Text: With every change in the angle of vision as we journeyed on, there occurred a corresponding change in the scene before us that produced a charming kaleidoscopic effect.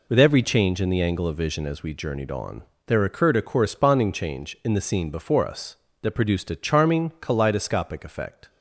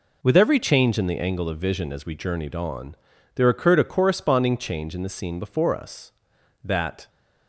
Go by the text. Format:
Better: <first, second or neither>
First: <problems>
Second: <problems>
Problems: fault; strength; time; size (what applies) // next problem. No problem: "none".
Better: first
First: none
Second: stops before "produced a charming kaleidoscopic effect"; at 7.0 s